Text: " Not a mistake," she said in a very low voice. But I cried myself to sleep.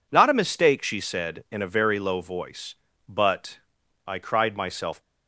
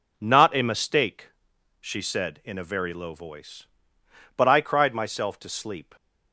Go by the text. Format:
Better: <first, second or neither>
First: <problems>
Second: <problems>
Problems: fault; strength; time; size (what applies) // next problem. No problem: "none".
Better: second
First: pauses between "But" and "I"; noticeable; at 3.5 s; 0.48 s long // stops before "to sleep"; at 5.0 s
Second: none